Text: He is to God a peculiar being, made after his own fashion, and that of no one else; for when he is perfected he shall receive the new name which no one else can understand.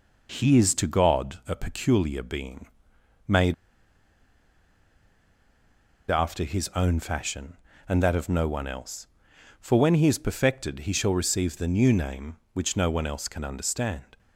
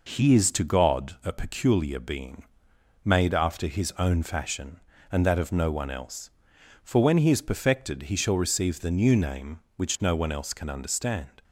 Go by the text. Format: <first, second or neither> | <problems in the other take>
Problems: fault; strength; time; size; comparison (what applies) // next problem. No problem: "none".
second | pauses between "made" and "after"; strong; at 3.5 s; 2.5 s long